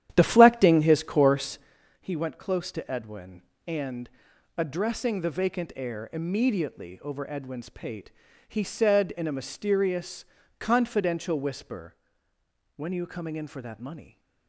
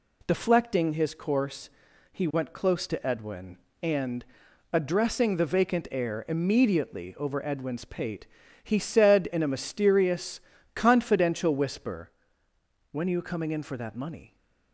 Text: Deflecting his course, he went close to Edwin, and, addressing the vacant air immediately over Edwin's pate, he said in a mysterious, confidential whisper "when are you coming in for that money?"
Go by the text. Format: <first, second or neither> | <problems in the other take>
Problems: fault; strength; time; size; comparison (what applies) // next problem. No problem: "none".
second | starts louder than the rest; strong; until 1.8 s; 11 dB // pauses between "whisper" and "when"; noticeable; at 11.9 s; 0.80 s long; noticeable in the second